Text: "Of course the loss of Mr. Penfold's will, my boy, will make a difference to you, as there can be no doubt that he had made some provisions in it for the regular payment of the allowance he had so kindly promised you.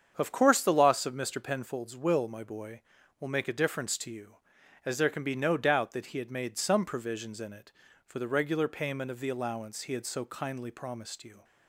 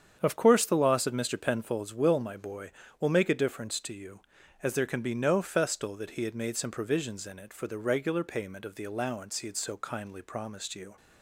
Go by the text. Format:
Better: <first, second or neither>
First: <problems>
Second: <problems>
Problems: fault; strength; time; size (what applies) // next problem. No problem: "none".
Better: first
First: starts louder than the rest; strong; until 1.1 s; 7.5 dB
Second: starts louder than the rest; strong; until 1.2 s; 8 dB // says "festal" for "doubt"; at 5.4 s